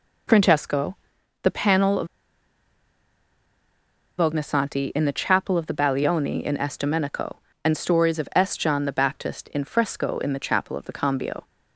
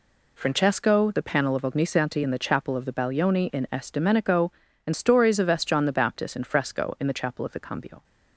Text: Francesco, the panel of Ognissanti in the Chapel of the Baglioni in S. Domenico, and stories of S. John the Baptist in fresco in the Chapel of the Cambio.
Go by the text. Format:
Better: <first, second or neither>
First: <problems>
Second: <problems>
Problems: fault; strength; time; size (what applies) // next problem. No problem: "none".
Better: second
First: pauses between "of" and "Ognissanti"; strong; at 2.0 s; 2.1 s long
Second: none